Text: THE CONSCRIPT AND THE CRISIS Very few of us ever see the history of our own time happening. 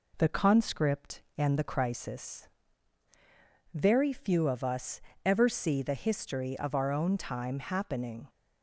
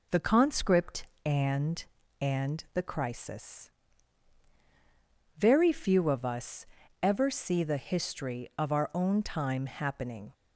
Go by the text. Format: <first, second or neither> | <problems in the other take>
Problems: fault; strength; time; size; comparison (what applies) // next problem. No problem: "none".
first | says "AND" twice; at 2.1 s // pauses between "CRISIS" and "Very"; strong; at 3.6 s; 1.6 s long; strong in the first // pauses between "us" and "ever"; at 6.6 s; 0.38 s long; slight in the first